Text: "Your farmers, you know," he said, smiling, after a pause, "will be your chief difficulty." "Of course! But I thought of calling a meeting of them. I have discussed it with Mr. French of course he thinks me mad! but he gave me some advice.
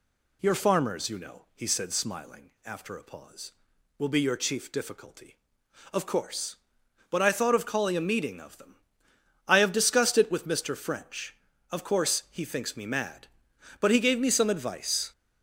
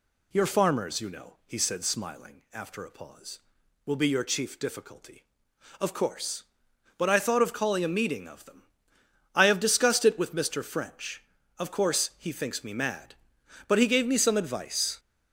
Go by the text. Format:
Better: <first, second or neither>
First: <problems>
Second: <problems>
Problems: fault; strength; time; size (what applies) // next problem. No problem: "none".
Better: neither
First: none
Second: none